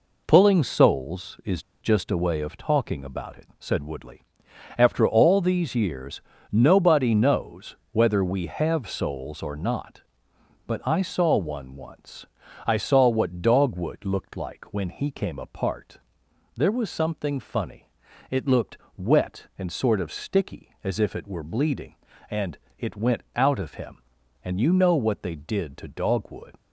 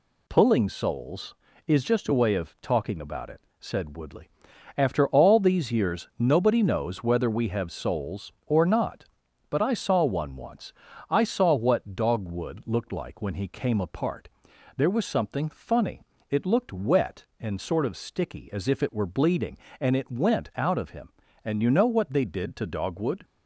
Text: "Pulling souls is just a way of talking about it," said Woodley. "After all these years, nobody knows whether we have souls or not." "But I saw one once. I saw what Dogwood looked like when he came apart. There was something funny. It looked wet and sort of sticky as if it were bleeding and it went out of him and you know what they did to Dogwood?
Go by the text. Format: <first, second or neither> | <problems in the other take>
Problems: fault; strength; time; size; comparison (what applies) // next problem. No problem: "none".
second | pauses between "is" and "just"; slight; at 1.6 s; 0.20 s long // pauses between "knows" and "whether"; slight; at 7.7 s; 0.16 s long // pauses between "looked" and "wet"; slight; at 18.7 s; 0.20 s long // pauses between "and" and "it"; slight; at 22.5 s; 0.20 s long // pauses between "went" and "out"; slight; at 23.2 s; 0.16 s long